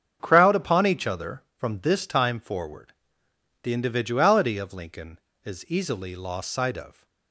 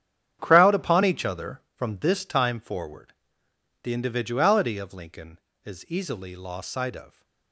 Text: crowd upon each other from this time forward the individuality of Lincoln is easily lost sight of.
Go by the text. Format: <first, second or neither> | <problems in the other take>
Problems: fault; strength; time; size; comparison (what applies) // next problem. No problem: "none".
first | gets quieter; strong; throughout; 12 dB // starts louder than the rest; strong; until 1.4 s; 9.5 dB; strong in the first // pauses between "forward" and "the"; noticeable; at 3.1 s; 0.70 s long; noticeable in the first